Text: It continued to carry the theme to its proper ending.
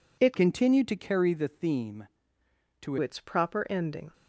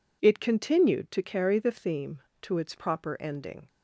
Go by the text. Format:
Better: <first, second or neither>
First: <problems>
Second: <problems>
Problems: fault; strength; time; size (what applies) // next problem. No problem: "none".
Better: second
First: changes voice from "continued" to "to"; from 0.3 to 2.9 s; 2.6 s long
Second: none